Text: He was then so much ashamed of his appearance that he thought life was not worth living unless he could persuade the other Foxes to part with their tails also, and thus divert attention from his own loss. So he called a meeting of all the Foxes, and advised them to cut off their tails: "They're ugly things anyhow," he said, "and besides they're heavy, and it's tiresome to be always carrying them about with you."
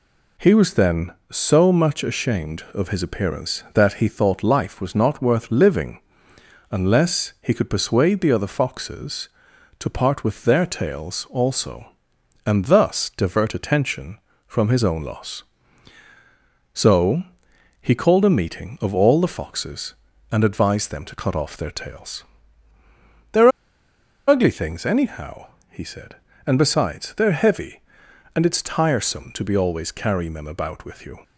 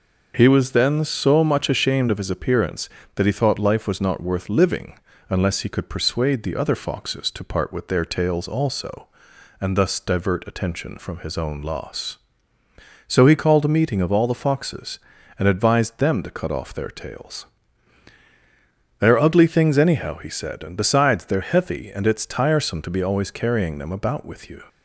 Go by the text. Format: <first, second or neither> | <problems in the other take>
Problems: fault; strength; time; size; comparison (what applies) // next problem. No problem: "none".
second | pauses between "living" and "unless"; noticeable; at 5.9 s; 0.70 s long; slight in the second // pauses between "So" and "he"; noticeable; at 17.2 s; 0.58 s long // pauses between "They're" and "ugly"; noticeable; at 23.4 s; 0.78 s long